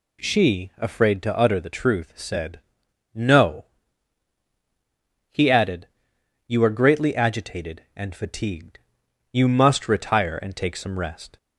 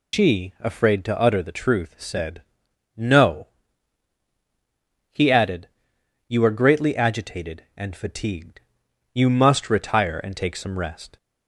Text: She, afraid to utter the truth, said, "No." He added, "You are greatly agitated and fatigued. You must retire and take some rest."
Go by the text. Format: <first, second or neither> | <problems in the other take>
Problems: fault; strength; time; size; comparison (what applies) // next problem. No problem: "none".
first | loses the start of "She"; at 0.1 s; 115 ms